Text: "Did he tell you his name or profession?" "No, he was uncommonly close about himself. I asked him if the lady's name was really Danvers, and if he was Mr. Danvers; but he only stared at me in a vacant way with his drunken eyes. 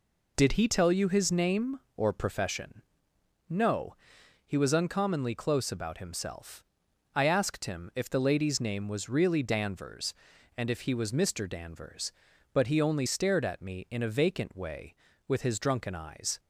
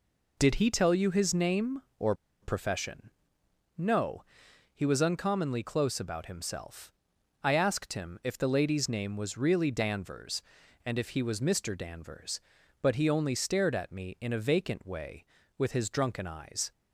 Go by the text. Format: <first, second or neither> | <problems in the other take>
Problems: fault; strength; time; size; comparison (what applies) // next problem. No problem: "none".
first | pauses between "or" and "profession"; slight; at 2.1 s; 0.28 s long